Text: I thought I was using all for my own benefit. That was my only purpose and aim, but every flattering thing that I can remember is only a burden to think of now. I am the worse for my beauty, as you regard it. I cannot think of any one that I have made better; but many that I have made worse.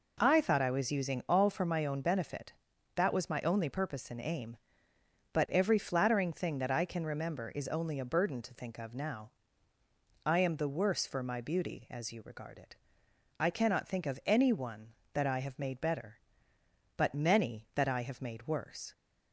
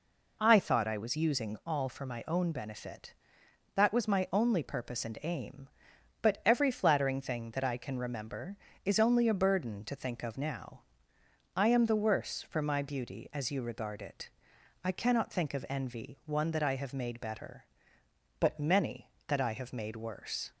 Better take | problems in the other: first | says "envy" for "any"; at 15.6 s

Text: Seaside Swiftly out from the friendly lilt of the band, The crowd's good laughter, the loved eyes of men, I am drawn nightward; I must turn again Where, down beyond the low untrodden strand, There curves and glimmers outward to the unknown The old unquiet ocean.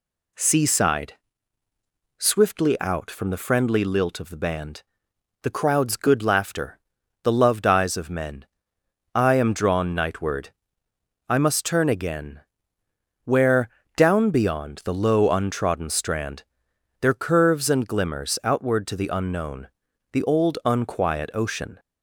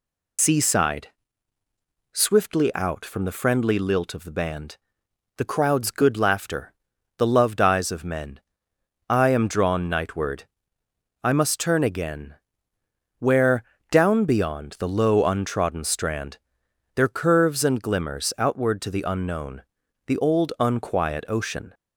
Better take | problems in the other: first | loses the start of "Seaside"; at 0.3 s; 90 ms // pauses between "Seaside" and "Swiftly"; at 1.0 s; 1.0 s long; also in the first // pauses between "again" and "Where"; noticeable; at 12.3 s; 0.86 s long; noticeable in the first // pauses between "unknown" and "The"; noticeable; at 19.6 s; 0.46 s long; noticeable in the first

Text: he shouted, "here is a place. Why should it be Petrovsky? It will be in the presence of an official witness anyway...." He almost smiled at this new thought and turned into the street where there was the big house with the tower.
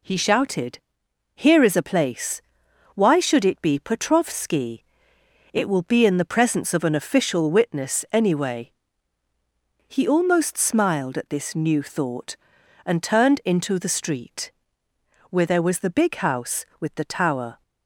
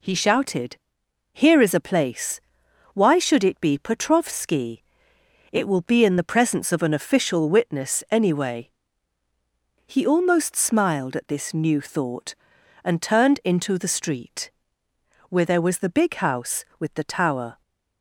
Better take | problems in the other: neither | pauses between "street" and "where"; noticeable; the same in both

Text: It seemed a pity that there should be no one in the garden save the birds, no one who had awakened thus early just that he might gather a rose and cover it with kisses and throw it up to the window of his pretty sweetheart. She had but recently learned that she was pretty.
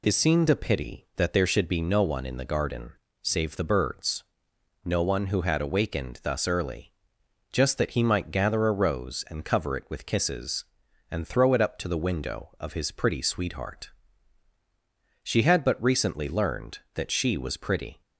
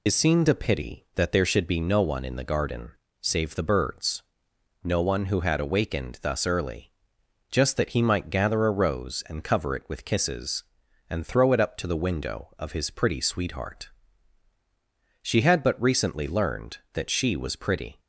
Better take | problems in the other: first | loses the start of "It"; at 0.0 s; 35 ms // pauses between "garden" and "save"; slight; at 2.8 s; 0.32 s long; slight in the first // pauses between "early" and "just"; noticeable; at 6.9 s; 0.60 s long; noticeable in the first

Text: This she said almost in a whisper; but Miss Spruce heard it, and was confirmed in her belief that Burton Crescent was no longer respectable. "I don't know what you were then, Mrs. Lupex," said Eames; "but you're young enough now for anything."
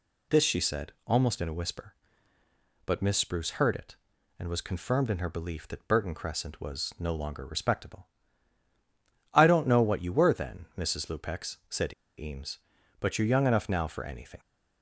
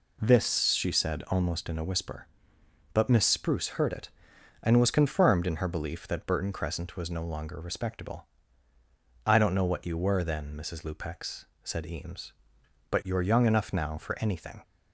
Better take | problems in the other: second | pauses between "said" and "Eames"; slight; at 11.9 s; 0.23 s long

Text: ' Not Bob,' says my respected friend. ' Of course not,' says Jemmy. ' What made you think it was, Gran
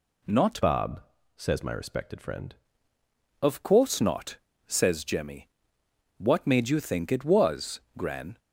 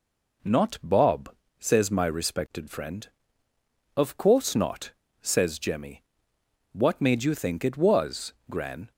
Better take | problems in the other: second | changes voice from "Bob" to "friend"; from 0.6 to 2.5 s; 1.9 s long

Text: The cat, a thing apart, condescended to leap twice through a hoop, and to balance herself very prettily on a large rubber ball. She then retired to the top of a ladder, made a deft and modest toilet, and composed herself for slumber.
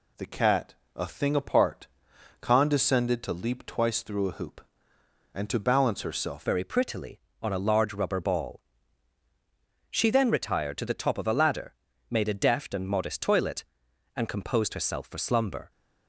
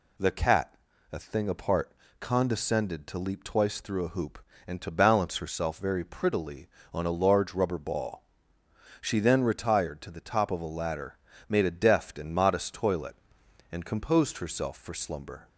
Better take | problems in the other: second | changes voice at "very"; from 6.4 s on; 9.3 s long

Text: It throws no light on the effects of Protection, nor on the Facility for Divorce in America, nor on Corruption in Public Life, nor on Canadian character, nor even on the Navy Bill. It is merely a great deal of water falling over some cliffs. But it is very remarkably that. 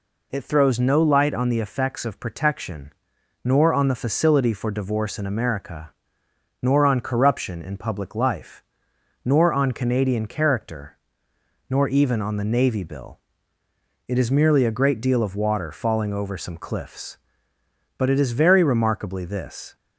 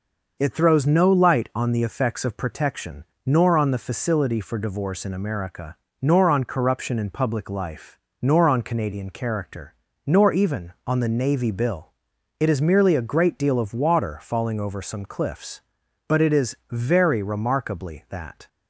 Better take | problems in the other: second | says "this" for "that"; at 19.2 s

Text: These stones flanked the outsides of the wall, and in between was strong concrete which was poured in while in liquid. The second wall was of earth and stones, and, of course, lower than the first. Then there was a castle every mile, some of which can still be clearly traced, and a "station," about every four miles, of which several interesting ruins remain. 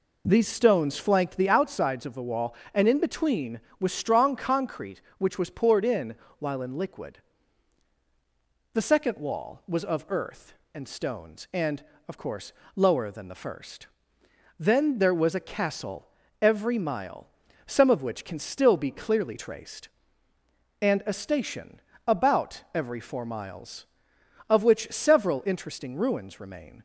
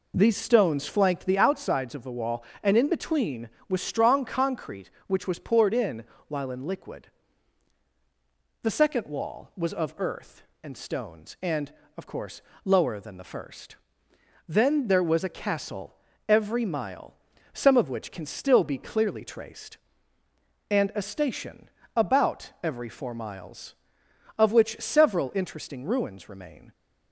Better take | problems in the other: neither | pauses between "in" and "while"; slight; the same in both // pauses between "castle" and "every"; slight; the same in both

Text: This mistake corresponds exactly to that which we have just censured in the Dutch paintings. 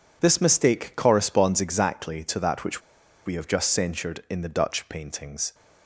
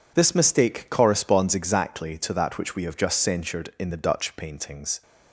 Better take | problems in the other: second | pauses between "which" and "we"; at 2.8 s; 0.45 s long

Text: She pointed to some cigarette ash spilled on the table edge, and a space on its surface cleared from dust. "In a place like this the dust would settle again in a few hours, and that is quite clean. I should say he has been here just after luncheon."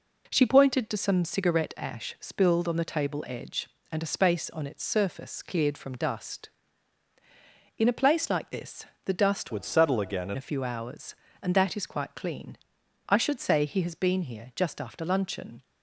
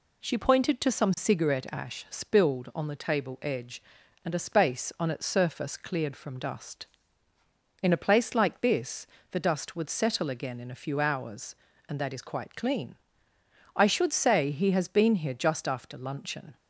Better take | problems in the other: second | pauses between "this" and "the"; slight; at 8.8 s; 0.20 s long; slight in the second // changes voice from "would" to "in"; from 9.4 to 10.3 s; 0.9 s long

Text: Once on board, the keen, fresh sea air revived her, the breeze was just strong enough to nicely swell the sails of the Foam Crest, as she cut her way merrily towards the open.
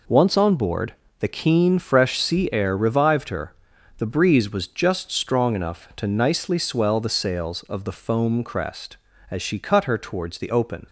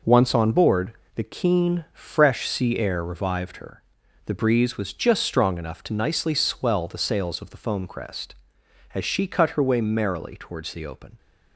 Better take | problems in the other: second | skips "way merrily"; at 9.9 s

